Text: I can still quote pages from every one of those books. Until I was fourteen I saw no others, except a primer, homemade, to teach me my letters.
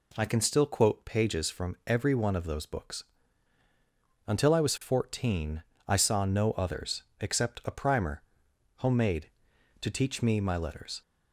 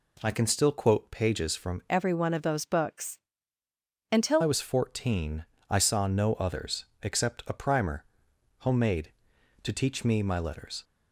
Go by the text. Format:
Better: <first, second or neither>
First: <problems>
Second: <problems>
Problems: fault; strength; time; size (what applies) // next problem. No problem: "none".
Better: first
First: pauses between "fourteen" and "I"; slight; at 5.6 s; 0.24 s long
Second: changes voice from "every" to "Until"; from 1.8 to 4.4 s; 2.6 s long // pauses between "fourteen" and "I"; slight; at 5.4 s; 0.24 s long